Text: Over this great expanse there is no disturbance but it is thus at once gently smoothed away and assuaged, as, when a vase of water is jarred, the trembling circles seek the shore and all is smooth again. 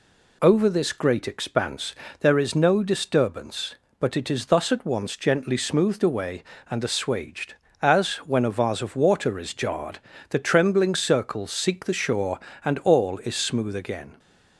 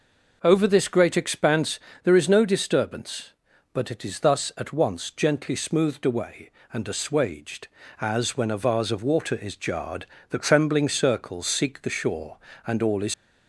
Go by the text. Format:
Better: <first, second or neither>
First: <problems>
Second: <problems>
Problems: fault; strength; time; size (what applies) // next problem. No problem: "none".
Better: first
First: pauses between "expanse" and "there"; slight; at 1.9 s; 0.26 s long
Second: pauses between "expanse" and "there"; slight; at 1.7 s; 0.24 s long // stops before "smooth again"; at 13.1 s